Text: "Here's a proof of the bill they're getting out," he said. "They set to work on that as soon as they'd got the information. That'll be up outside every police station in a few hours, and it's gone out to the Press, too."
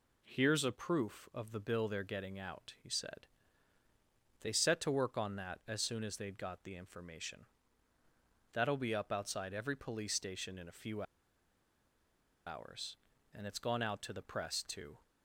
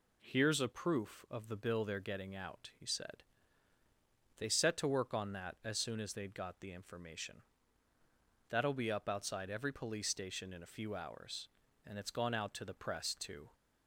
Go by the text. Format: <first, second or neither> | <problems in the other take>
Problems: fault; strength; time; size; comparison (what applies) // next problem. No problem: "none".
second | pauses between "few" and "hours"; strong; at 11.0 s; 1.4 s long